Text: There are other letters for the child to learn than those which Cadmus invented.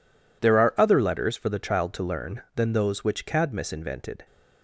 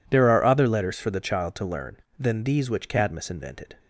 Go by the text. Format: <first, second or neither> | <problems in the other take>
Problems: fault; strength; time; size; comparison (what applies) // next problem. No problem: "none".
first | says "these" for "those"; at 2.4 s